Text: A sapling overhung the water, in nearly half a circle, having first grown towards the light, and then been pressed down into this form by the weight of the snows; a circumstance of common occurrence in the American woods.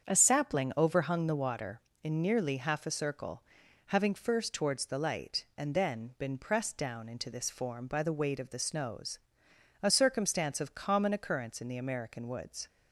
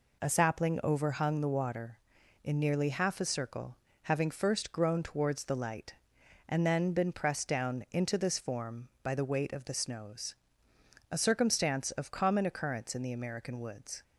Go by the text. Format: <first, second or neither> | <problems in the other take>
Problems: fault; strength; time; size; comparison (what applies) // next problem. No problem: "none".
second | starts louder than the rest; strong; until 1.0 s; 7.5 dB // skips "grown"; at 4.5 s